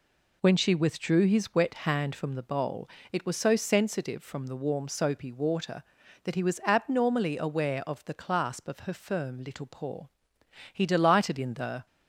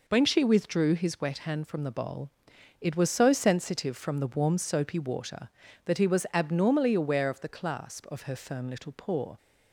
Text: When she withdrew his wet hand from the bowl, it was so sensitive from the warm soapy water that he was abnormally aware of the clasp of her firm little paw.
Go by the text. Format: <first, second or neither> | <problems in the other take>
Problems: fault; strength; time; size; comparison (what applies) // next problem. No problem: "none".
second | goes on to say "He delighted in the"; noticeable; from 10.7 s on; 1.1 s long